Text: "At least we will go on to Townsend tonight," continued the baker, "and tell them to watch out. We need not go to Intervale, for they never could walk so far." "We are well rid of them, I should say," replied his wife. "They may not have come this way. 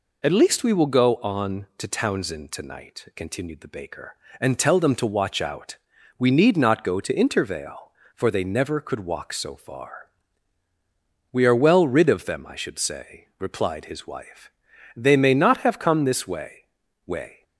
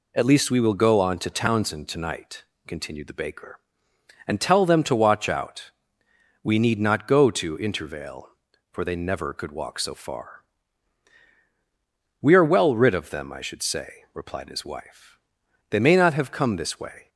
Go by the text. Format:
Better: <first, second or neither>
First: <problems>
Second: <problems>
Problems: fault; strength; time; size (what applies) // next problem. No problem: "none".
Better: second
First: says "way" twice; at 17.0 s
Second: none